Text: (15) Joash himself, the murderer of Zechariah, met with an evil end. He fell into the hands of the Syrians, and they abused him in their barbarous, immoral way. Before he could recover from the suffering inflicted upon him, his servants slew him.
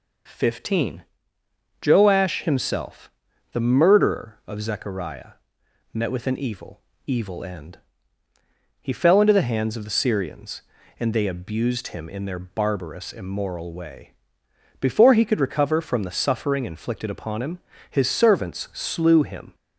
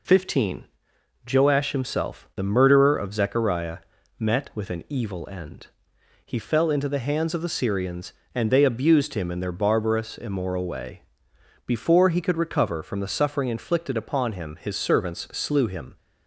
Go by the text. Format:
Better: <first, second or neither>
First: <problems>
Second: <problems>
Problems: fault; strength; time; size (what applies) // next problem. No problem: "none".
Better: second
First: says "evil" twice; at 7.0 s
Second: none